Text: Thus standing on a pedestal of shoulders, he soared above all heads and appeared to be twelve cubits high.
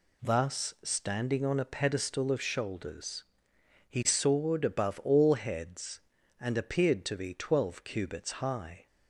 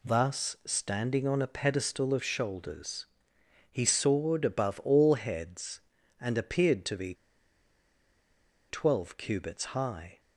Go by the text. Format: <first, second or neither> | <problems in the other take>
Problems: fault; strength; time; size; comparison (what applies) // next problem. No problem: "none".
first | pauses between "be" and "twelve"; strong; at 7.1 s; 1.5 s long